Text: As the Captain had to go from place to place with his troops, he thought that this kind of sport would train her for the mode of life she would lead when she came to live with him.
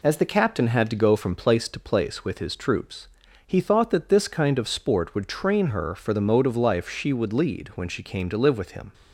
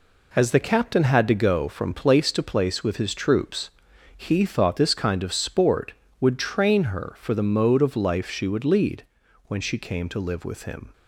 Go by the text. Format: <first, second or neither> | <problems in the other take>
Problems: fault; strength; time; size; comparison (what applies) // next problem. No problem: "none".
first | skips "that"; at 4.7 s // pauses between "lead" and "when"; noticeable; at 9.0 s; 0.46 s long